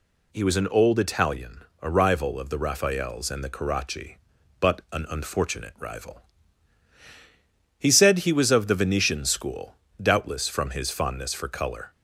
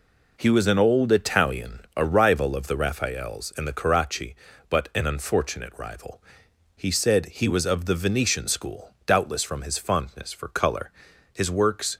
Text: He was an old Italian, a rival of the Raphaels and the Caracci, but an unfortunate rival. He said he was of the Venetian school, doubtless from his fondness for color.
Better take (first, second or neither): first